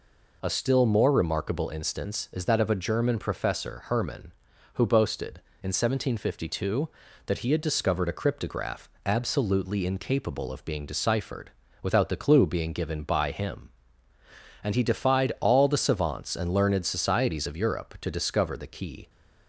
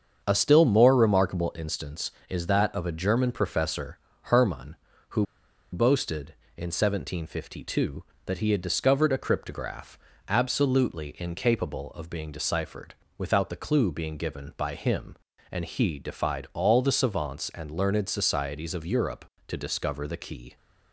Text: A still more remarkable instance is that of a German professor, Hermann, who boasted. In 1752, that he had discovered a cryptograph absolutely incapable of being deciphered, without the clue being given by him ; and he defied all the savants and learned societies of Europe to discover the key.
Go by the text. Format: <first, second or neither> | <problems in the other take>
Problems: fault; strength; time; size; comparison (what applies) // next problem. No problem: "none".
first | starts louder than the rest; strong; until 1.2 s; 7 dB // pauses between "who" and "boasted"; noticeable; at 5.2 s; 0.48 s long // pauses between "cryptograph" and "absolutely"; slight; at 9.9 s; 0.30 s long; slight in the first